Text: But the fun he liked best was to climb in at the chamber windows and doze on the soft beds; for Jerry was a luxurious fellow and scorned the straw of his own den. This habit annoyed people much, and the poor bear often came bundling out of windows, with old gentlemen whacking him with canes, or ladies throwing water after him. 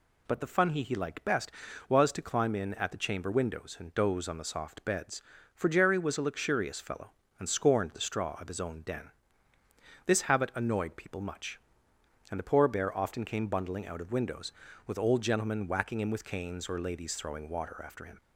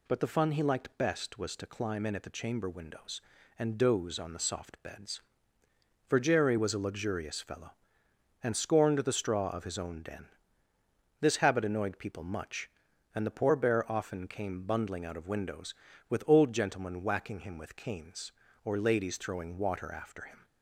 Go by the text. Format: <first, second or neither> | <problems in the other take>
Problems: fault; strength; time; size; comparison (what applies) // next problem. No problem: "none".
second | says "he" twice; at 0.8 s